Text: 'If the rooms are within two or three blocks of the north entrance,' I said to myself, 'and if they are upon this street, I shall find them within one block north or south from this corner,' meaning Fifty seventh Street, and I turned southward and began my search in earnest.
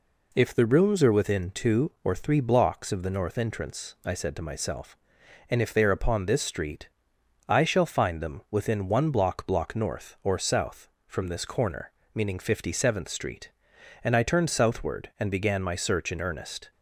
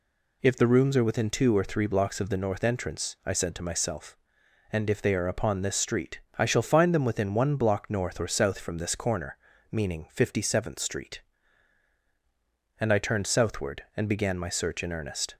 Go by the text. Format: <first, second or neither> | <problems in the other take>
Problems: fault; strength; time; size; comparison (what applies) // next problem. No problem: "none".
second | says "block" twice; at 9.4 s